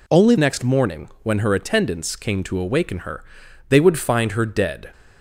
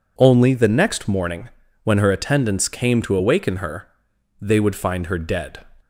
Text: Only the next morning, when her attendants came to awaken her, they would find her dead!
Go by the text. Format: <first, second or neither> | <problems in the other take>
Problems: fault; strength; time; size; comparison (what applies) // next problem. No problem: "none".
second | skips "the"; at 0.3 s